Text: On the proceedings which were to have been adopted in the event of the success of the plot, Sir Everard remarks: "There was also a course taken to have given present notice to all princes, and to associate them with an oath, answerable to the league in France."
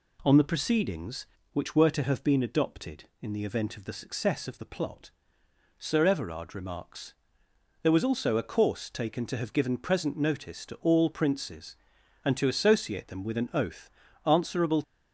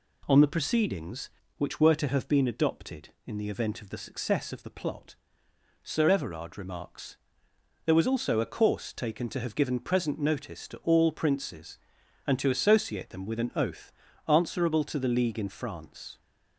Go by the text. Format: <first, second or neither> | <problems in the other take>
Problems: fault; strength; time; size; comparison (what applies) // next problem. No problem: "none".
second | stops before "to the league in France"; at 14.8 s